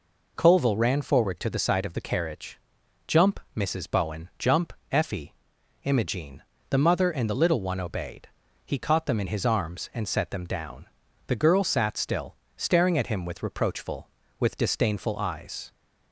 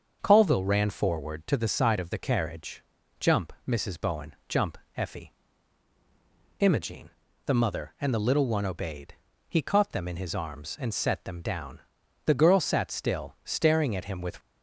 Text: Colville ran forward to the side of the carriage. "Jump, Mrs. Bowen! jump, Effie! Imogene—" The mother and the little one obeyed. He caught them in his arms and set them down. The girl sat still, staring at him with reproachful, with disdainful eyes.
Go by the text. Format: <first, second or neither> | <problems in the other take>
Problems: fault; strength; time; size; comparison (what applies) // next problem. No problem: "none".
first | starts louder than the rest; until 1.2 s; 6.5 dB // stops before "reproachful with disdainful eyes"; at 14.4 s